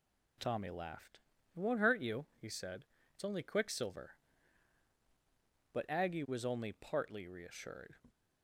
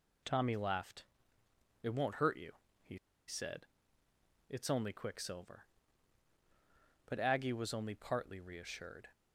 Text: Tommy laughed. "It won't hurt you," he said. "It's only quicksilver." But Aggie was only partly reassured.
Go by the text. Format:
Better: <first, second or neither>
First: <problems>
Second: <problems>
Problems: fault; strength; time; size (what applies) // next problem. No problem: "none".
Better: first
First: none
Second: pauses between "he" and "said"; slight; at 2.9 s; 0.31 s long